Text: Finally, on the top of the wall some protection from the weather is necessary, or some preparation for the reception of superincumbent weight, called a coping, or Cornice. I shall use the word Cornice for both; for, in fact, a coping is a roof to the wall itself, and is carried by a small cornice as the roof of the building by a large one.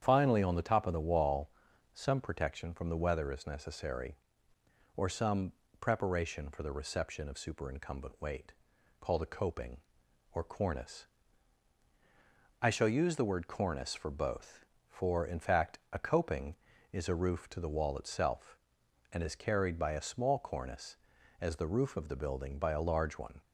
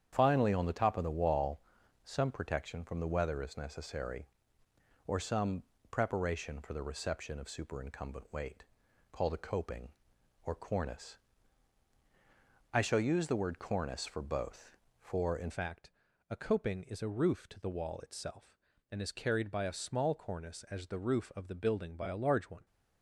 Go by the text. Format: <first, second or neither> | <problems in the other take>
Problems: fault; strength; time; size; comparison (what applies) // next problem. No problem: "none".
first | starts louder than the rest; strong; until 1.1 s; 8.5 dB; strong in the first // pauses between "wall" and "some"; at 1.5 s; 0.44 s long; also in the first // pauses between "some" and "preparation"; slight; at 5.6 s; 0.26 s long; slight in the first // changes voice at "fact"; from 15.4 s on; 7.2 s long